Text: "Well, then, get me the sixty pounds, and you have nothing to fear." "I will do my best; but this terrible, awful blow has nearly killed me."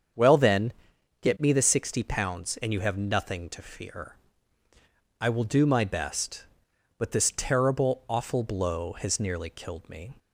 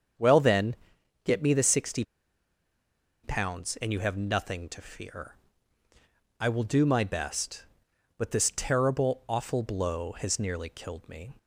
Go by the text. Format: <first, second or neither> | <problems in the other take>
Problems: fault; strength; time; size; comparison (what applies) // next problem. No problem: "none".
first | starts louder than the rest; strong; until 1.6 s; 7 dB; strong in the first // pauses between "sixty" and "pounds"; at 2.0 s; 1.2 s long